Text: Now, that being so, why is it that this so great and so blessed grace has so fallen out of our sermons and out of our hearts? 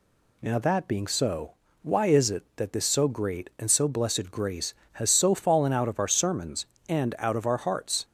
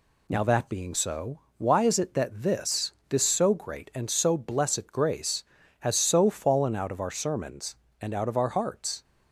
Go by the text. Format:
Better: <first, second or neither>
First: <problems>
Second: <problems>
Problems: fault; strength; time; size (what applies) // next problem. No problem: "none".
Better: first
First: none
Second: says "this" twice; at 3.0 s